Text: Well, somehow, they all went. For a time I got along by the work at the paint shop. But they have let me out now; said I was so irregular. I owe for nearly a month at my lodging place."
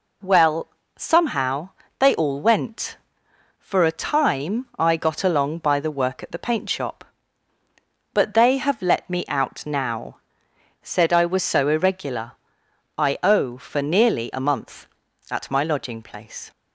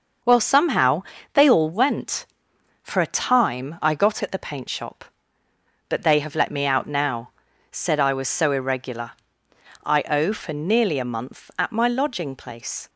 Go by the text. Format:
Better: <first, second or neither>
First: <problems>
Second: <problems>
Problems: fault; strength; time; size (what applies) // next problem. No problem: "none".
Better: first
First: none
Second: starts louder than the rest; noticeable; until 1.5 s; 6 dB // skips "along by the work"; at 4.2 s